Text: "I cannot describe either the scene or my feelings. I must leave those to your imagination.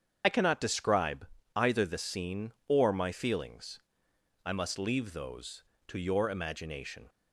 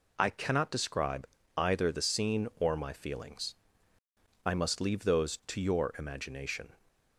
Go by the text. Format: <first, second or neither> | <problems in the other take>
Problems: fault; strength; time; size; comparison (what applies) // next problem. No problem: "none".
second | loses the start of "I"; at 0.2 s; 40 ms // starts louder than the rest; strong; until 1.2 s; 7.5 dB // pauses between "describe" and "either"; slight; at 1.2 s; 0.30 s long; slight in the second